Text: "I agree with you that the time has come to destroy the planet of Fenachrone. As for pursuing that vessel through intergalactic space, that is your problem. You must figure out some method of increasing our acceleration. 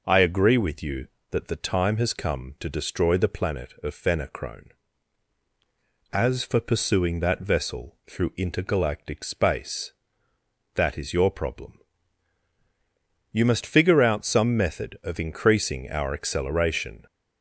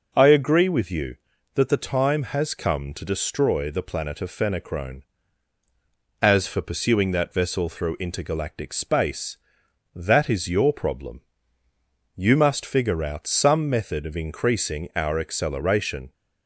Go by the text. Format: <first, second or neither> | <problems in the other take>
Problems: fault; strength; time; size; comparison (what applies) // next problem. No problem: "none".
neither | none